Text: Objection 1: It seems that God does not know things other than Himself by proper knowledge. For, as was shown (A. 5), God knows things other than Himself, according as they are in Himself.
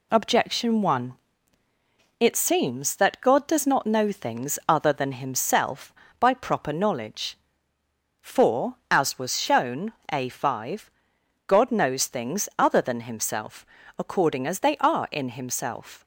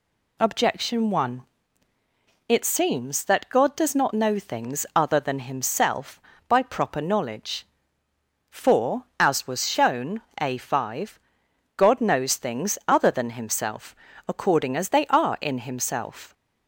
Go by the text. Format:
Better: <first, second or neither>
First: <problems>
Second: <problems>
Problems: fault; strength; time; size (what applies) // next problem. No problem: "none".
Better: second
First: gets quieter; noticeable; throughout; 4 dB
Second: none